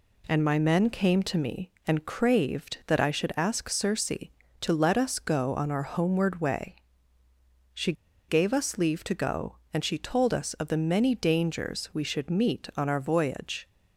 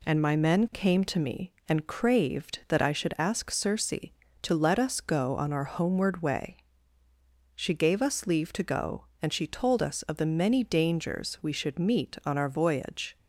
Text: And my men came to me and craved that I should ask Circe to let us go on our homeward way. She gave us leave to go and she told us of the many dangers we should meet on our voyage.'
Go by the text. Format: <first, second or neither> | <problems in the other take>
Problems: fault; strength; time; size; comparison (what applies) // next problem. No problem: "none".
second | pauses between "She" and "gave"; slight; at 7.9 s; 0.35 s long